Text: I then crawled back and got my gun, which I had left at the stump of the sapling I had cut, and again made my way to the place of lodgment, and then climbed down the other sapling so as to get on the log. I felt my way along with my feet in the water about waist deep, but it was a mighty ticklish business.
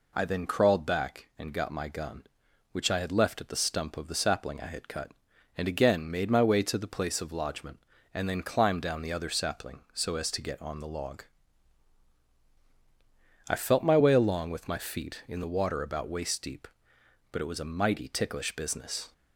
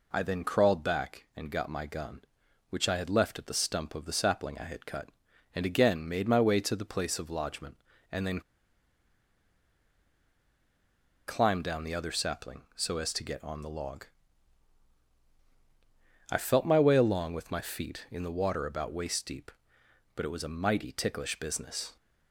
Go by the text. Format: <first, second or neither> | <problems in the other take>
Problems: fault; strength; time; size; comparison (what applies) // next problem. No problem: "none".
first | pauses between "then" and "climbed"; strong; at 8.3 s; 2.8 s long